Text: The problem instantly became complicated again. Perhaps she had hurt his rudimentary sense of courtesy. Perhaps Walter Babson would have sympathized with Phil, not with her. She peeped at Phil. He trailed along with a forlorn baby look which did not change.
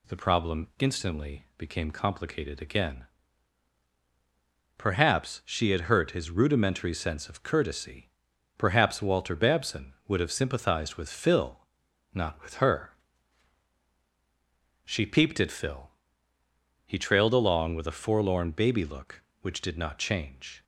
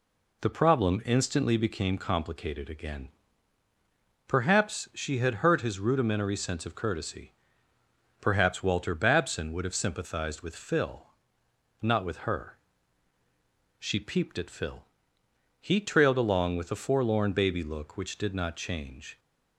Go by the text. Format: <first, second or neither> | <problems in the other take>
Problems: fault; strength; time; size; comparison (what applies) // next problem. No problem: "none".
neither | none